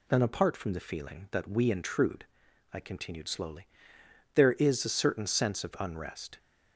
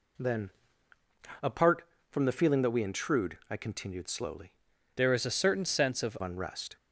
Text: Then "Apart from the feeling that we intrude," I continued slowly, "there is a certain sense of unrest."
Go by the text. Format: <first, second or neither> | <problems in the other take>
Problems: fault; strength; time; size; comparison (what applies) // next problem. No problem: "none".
first | pauses between "Then" and "Apart"; noticeable; at 0.4 s; 0.94 s long // changes voice from "there" to "of"; from 4.9 to 6.1 s; 1.2 s long